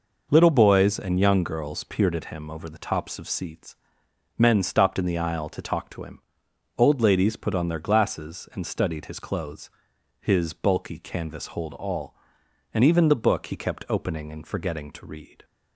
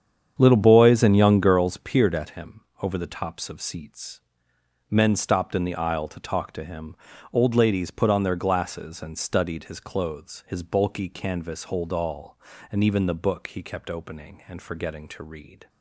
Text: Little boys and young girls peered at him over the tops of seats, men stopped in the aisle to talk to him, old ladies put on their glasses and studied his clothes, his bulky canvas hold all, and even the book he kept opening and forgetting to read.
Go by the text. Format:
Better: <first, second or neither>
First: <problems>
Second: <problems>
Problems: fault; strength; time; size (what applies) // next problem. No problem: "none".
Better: first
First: none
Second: starts louder than the rest; strong; until 1.7 s; 8 dB // pauses between "him" and "over"; slight; at 2.6 s; 0.22 s long